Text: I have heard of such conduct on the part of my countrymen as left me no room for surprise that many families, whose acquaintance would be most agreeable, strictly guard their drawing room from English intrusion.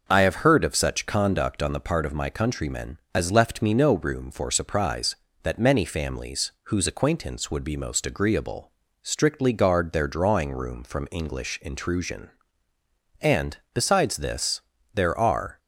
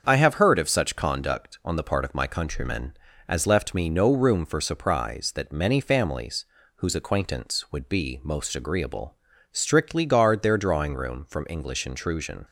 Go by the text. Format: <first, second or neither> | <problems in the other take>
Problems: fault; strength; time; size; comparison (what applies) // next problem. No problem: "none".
second | starts louder than the rest; noticeable; until 1.0 s; 6 dB; also in the second // goes on to say "And besides this there are"; strong; from 13.2 s on; 2.3 s long